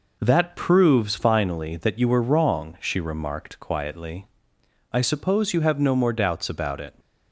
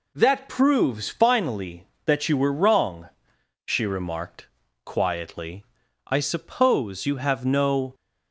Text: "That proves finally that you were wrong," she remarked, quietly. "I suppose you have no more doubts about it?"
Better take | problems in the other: first | stops before "more doubts about it"; at 7.9 s

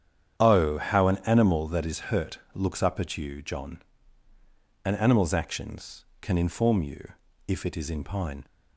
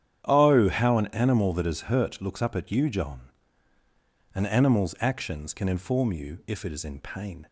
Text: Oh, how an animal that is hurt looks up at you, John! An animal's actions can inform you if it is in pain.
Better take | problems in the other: second | starts louder than the rest; strong; until 1.4 s; 9 dB; strong in the second // pauses between "hurt" and "looks"; slight; at 2.3 s; 0.16 s long // pauses between "you" and "if"; slight; at 7.1 s; 0.34 s long // says "pine" for "pain"; at 8.0 s

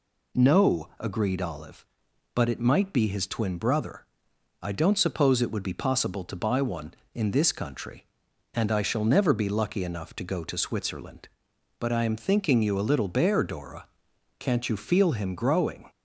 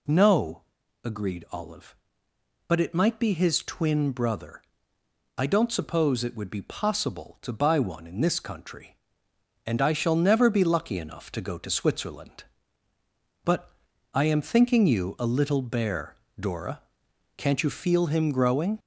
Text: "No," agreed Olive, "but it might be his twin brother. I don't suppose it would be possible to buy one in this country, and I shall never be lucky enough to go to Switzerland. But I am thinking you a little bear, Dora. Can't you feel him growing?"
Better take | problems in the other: first | gets louder; throughout; 3.5 dB // pauses between "But" and "I"; at 13.7 s; 0.42 s long

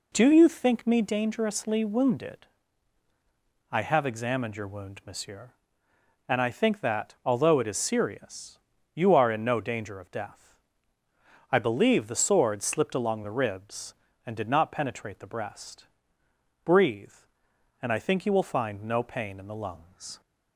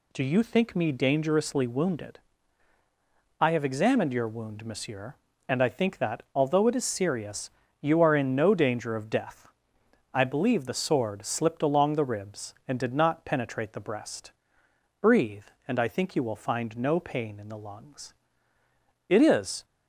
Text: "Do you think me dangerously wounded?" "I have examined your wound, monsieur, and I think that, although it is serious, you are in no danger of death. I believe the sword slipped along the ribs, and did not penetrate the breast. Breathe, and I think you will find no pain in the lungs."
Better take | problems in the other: first | goes on to say "It is"; from 19.0 s on; 0.56 s long

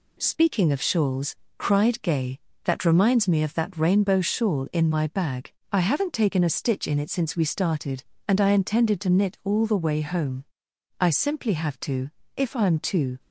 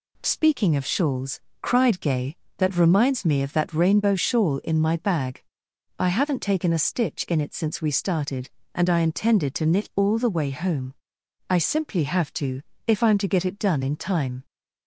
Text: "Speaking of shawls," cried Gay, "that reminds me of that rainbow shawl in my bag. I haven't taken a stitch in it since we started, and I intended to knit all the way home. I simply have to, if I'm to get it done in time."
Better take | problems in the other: second | stops before "get it done in time"; at 13.1 s

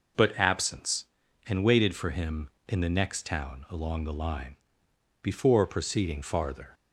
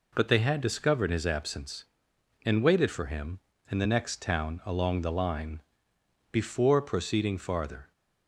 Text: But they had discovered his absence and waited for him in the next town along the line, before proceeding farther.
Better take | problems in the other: second | skips "they had discovered his"; at 0.3 s

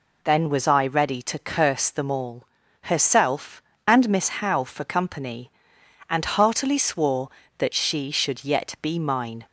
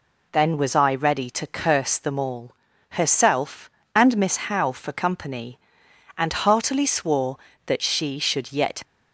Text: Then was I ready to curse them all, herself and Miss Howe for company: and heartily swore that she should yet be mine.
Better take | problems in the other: first | stops before "be mine"; at 8.8 s

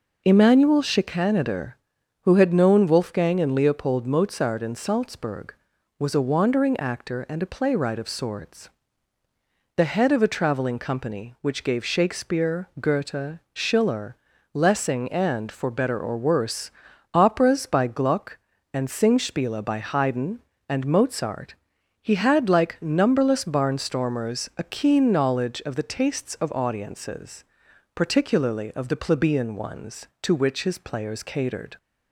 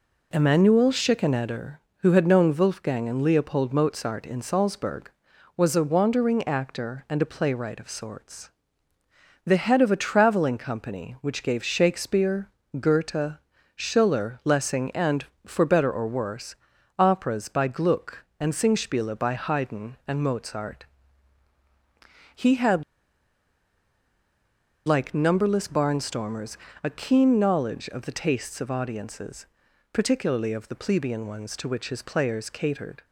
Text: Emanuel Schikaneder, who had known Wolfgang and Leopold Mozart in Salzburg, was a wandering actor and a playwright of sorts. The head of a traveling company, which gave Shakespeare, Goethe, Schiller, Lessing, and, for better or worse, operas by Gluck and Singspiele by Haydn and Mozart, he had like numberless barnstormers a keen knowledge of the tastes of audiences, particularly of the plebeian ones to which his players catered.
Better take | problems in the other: first | pauses between "had" and "like"; strong; at 22.8 s; 2.0 s long // pauses between "barnstormers" and "a"; slight; at 26.5 s; 0.26 s long

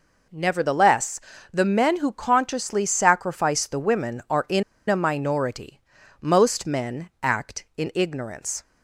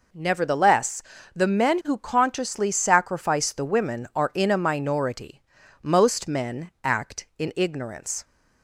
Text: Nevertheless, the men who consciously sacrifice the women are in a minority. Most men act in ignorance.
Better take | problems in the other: second | pauses between "in" and "a"; slight; at 4.6 s; 0.27 s long

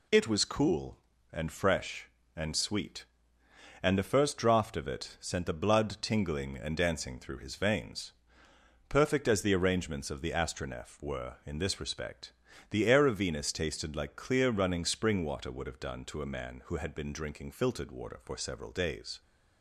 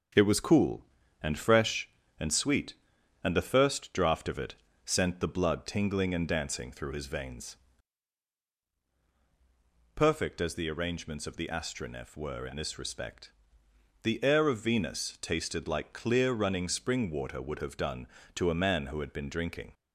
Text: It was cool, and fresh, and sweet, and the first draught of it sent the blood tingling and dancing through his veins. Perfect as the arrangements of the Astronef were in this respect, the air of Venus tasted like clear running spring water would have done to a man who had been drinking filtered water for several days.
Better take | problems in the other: first | starts louder than the rest; strong; until 1.5 s; 7.5 dB // pauses between "it" and "sent"; slight; at 4.5 s; 0.32 s long // stops before "filtered water for several days"; at 19.7 s

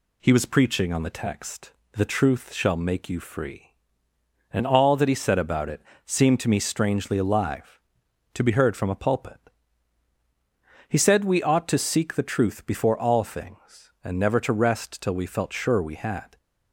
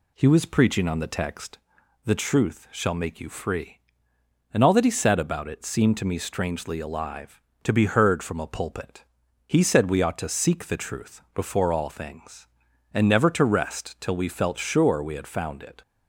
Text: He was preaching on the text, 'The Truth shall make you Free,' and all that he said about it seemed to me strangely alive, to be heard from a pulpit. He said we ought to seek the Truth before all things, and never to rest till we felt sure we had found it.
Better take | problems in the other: second | pauses between "it" and "seemed"; slight; at 5.8 s; 0.24 s long // stops before "found it"; at 16.3 s

